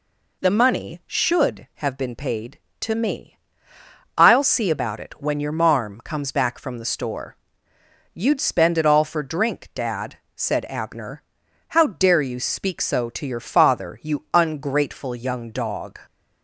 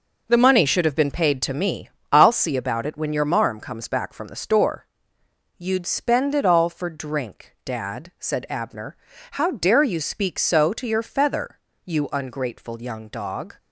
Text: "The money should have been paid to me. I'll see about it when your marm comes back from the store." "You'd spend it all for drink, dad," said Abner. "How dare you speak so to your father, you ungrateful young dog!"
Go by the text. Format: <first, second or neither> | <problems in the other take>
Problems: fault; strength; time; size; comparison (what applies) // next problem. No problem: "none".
first | says "feather" for "father"; at 11.0 s